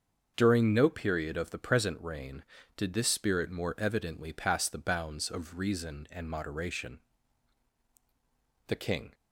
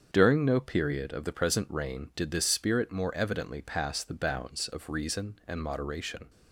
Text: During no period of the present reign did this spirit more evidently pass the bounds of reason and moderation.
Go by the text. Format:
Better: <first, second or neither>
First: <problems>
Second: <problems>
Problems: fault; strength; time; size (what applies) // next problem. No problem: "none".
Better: second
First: starts louder than the rest; until 1.3 s; 6.5 dB // goes on to say "The king"; slight; from 8.6 s on; 0.46 s long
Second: starts louder than the rest; strong; until 1.1 s; 7 dB